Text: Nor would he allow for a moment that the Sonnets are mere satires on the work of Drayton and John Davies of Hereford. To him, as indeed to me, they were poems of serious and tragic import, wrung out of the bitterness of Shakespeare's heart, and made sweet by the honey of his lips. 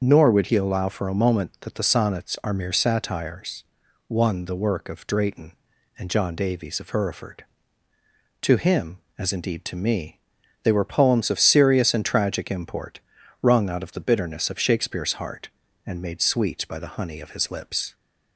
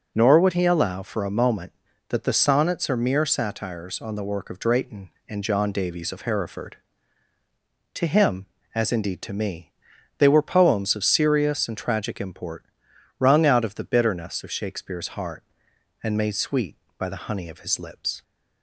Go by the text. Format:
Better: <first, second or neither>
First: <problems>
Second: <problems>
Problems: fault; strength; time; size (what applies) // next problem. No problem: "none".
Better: second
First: starts louder than the rest; until 1.0 s; 6.5 dB // says "one" for "on"; at 4.0 s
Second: none